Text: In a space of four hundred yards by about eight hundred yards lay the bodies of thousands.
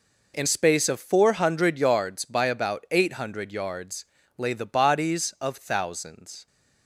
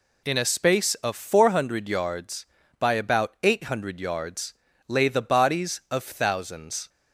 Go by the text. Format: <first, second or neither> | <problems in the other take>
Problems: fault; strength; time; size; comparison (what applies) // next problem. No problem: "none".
second | skips "a"; at 0.4 s // pauses between "yards" and "lay"; slight; at 4.0 s; 0.32 s long; slight in the second